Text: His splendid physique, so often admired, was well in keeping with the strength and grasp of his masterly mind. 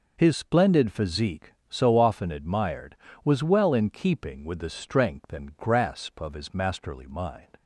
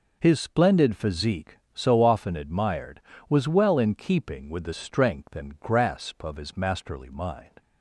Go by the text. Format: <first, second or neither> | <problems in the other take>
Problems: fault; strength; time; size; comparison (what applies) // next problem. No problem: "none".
neither | none